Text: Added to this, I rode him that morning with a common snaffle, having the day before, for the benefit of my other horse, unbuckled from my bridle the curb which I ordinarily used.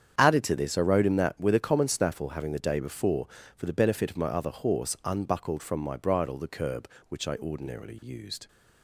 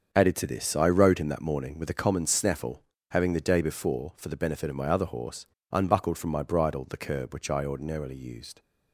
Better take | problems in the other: second | starts louder than the rest; strong; until 1.1 s; 8.5 dB; also in the second // skips "morning"; at 1.3 s

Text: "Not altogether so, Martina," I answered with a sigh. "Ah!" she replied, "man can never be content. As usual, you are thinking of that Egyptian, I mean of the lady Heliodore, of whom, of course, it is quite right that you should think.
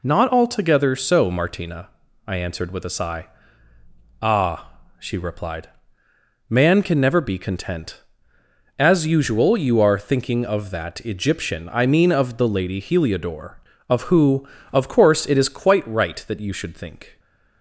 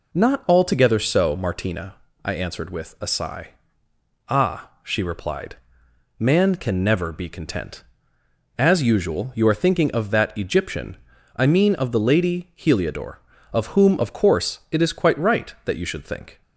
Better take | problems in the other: second | says "who" for "whom"; at 14.0 s

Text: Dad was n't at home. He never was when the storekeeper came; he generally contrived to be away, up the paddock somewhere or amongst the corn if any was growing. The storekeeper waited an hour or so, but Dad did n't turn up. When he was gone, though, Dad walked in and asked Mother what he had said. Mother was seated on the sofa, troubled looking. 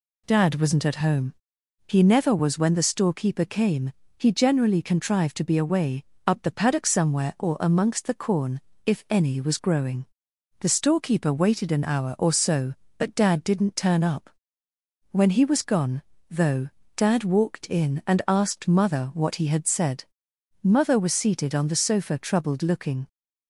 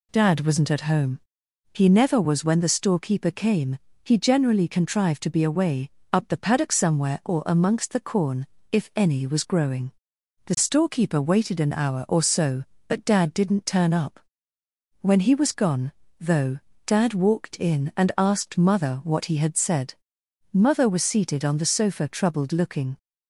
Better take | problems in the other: neither | pauses between "corn" and "if"; slight; the same in both

